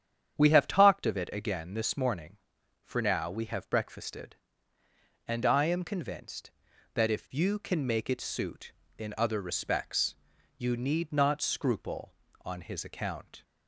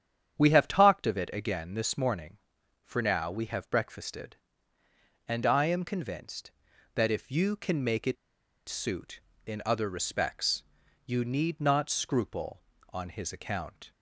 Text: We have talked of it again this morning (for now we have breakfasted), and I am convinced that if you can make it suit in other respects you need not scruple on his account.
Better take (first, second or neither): first